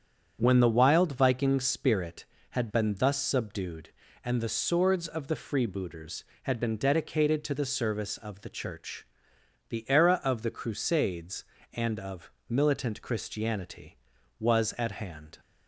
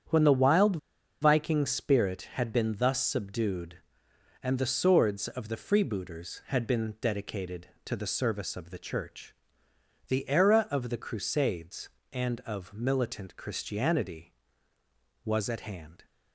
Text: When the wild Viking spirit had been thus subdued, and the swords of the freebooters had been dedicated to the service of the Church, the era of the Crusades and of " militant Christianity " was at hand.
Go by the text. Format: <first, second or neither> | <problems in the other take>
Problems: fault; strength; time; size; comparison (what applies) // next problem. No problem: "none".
first | starts louder than the rest; strong; until 1.5 s; 8.5 dB; strong in the first // pauses between "wild" and "Viking"; at 0.7 s; 0.44 s long